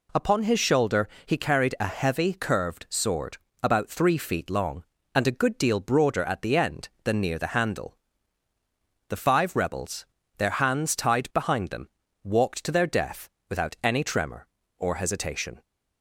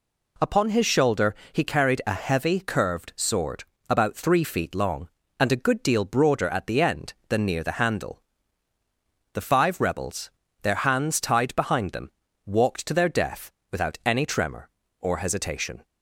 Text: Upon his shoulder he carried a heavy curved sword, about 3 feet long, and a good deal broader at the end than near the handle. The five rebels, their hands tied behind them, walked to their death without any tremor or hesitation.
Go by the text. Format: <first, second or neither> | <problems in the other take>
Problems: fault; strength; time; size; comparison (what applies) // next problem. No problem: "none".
neither | pauses between "shoulder" and "he"; slight; the same in both // pauses between "death" and "without"; slight; the same in both